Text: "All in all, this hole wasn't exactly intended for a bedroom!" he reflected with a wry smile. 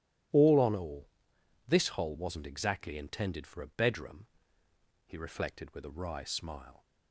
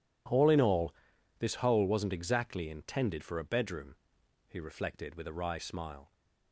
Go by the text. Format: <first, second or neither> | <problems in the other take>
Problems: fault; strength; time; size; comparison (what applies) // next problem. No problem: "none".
second | starts louder than the rest; strong; until 1.9 s; 13 dB // says "on" for "in"; at 0.5 s